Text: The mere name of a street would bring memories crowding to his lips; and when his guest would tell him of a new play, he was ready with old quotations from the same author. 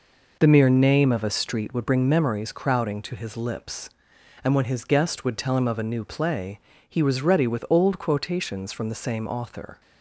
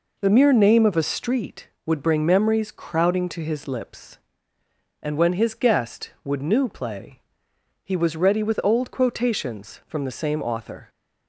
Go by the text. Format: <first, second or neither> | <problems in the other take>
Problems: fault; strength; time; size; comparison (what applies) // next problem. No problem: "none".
first | skips "tell him of a"; at 6.4 s